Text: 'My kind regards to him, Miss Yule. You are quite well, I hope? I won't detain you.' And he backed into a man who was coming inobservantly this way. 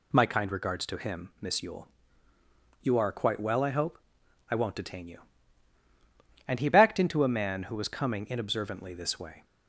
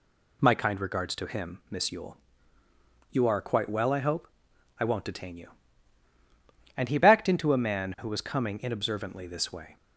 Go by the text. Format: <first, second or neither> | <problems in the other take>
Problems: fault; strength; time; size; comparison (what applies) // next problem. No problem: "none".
neither | none